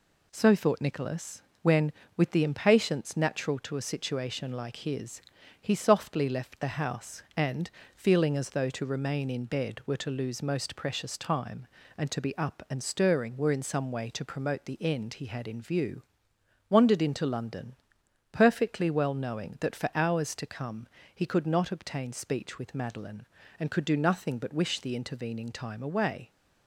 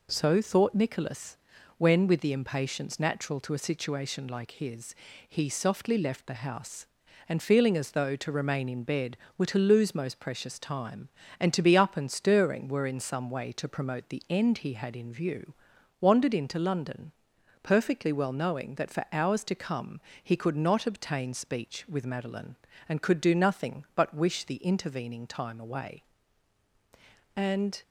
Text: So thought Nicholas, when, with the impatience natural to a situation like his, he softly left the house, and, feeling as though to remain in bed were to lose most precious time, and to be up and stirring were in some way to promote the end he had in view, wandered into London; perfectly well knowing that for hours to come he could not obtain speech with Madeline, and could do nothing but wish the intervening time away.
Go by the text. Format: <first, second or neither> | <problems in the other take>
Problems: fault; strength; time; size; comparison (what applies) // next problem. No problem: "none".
first | pauses between "come" and "he"; slight; at 19.9 s; 0.24 s long; slight in the first // goes on to say "And"; slight; from 27.3 s on; 0.44 s long